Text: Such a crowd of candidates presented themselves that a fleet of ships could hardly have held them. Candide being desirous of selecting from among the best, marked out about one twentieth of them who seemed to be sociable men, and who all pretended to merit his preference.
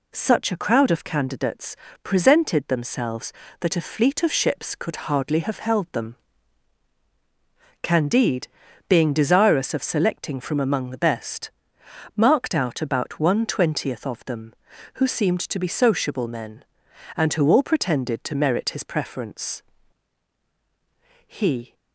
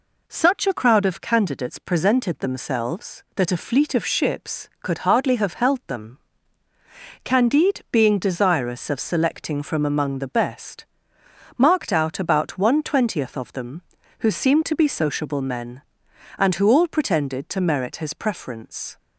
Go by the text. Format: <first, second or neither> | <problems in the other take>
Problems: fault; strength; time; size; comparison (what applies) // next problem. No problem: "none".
second | pauses between "candidates" and "presented"; slight; at 1.7 s; 0.28 s long // pauses between "Candide" and "being"; at 8.4 s; 0.42 s long // goes on to say "He"; slight; from 21.2 s on; 0.48 s long